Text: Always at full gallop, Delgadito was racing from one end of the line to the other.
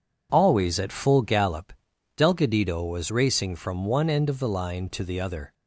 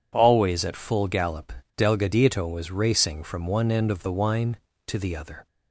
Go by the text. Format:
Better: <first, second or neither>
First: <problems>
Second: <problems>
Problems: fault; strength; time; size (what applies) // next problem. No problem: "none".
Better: first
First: none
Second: says "wine" for "line"; at 4.1 s